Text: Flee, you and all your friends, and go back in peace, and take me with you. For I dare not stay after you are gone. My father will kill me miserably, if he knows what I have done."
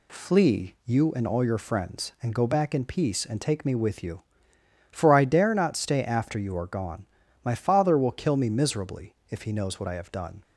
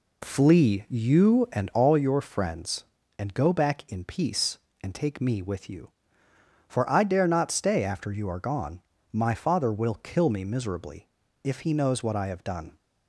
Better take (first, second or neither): first